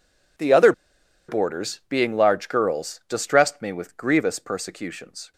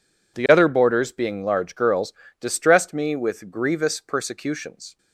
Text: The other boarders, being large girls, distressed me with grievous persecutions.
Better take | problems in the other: second | pauses between "other" and "boarders"; noticeable; at 0.7 s; 0.56 s long

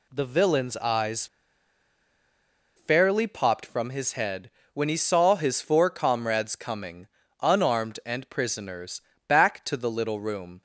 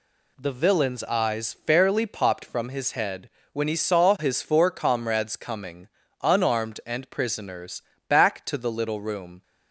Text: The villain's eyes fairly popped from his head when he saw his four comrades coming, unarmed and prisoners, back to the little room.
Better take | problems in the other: second | pauses between "eyes" and "fairly"; strong; at 1.2 s; 1.5 s long // pauses between "head" and "when"; slight; at 4.4 s; 0.24 s long; slight in the second

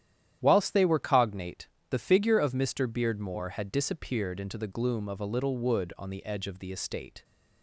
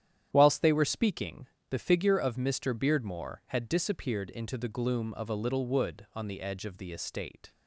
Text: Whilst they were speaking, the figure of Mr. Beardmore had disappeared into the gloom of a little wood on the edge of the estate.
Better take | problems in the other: second | starts louder than the rest; strong; until 1.4 s; 11 dB; strong in the second // says "cognate" for "speaking"; at 0.9 s

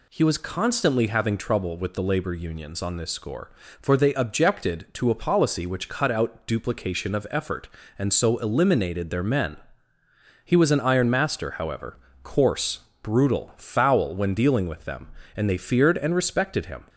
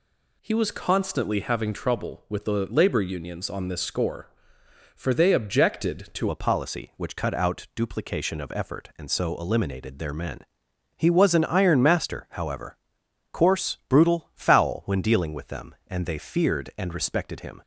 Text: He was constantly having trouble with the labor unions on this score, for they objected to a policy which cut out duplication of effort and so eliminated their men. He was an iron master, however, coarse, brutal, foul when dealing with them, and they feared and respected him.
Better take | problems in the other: first | changes voice at "a"; from 6.2 s on; 11.4 s long

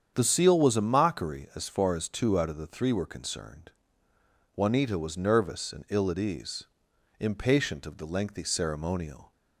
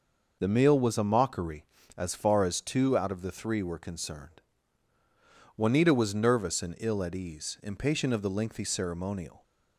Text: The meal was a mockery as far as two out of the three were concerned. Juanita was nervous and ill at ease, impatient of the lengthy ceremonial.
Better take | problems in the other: second | starts louder than the rest; strong; until 1.1 s; 8 dB // says "seal" for "meal"; at 0.2 s

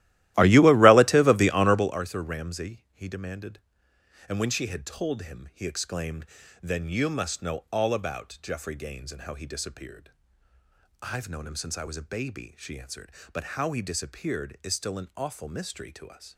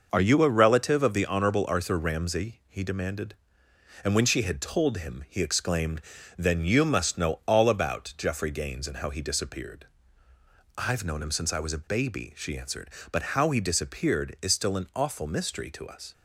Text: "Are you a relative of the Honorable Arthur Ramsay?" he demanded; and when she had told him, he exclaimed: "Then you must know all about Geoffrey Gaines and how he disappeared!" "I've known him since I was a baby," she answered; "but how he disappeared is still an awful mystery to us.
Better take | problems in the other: second | starts louder than the rest; strong; until 2.0 s; 15.5 dB

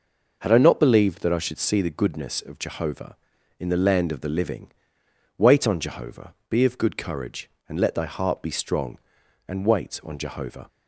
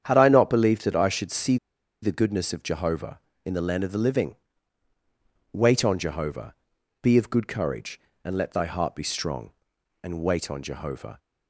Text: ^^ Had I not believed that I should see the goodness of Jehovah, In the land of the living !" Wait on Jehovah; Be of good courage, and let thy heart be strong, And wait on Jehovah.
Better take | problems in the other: first | starts louder than the rest; strong; until 1.0 s; 9 dB // pauses between "see" and "the"; at 1.5 s; 0.45 s long

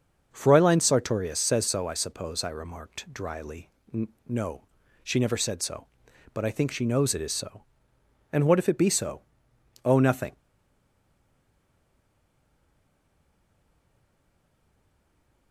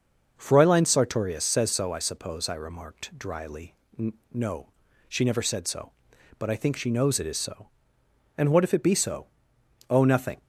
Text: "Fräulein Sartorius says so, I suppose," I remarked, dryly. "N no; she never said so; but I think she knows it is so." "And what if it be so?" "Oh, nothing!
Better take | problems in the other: second | starts louder than the rest; noticeable; until 1.3 s; 6 dB; also in the second // pauses between "N" and "no"; slight; at 4.0 s; 0.20 s long; slight in the second // stays silent after the last word; strong; from 10.3 s on; 5.2 s long

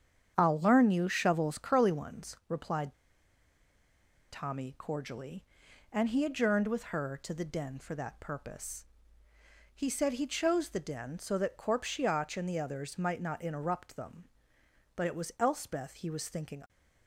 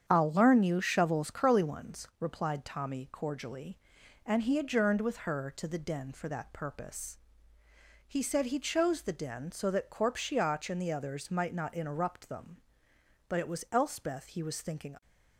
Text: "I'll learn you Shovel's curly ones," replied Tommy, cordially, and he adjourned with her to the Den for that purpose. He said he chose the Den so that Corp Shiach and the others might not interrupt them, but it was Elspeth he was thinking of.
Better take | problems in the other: second | starts louder than the rest; strong; until 1.3 s; 8.5 dB; strong in the second // pauses between "replied" and "Tommy"; strong; at 2.9 s; 1.3 s long

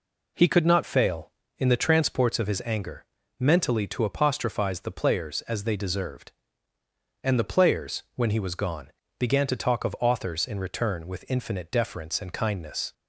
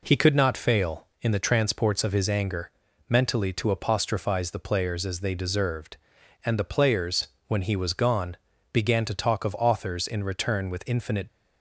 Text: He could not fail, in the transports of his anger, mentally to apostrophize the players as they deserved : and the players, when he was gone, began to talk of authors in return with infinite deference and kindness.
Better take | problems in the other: first | stops before "deference and kindness"; at 11.2 s

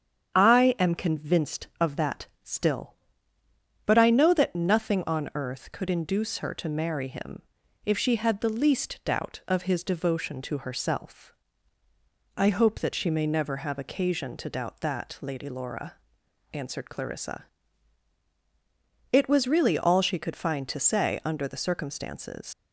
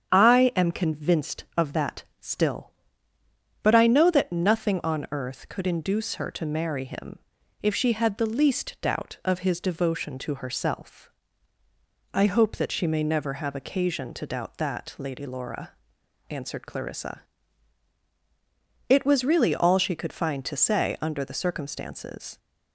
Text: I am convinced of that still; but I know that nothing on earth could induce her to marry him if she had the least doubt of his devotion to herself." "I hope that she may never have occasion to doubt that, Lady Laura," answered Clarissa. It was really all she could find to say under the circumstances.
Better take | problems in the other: second | starts louder than the rest; strong; until 1.3 s; 8 dB; strong in the second // pauses between "that" and "still"; slight; at 2.2 s; 0.16 s long; slight in the second // pauses between "him" and "if"; at 7.4 s; 0.42 s long; also in the second // leaves "circumstances" unfinished; at 22.5 s; 80 ms

